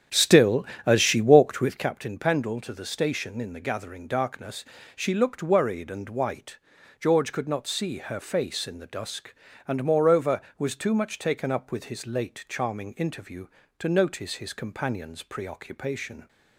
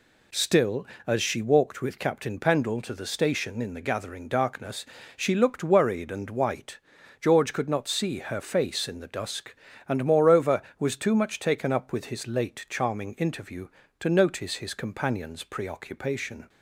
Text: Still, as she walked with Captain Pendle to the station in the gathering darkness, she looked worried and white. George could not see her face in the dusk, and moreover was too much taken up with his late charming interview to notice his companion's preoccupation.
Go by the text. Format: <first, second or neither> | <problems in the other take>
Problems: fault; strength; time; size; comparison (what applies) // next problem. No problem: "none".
second | starts louder than the rest; strong; until 2.0 s; 8.5 dB